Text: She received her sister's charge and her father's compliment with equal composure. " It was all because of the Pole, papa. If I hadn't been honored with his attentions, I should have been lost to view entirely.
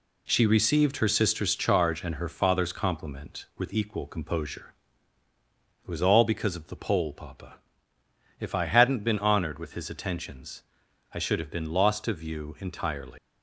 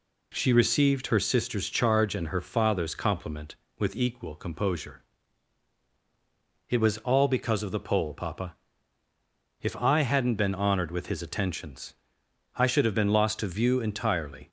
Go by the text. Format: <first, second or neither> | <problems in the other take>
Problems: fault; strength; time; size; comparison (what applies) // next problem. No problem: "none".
second | leaves "entirely" unfinished; at 13.1 s; 185 ms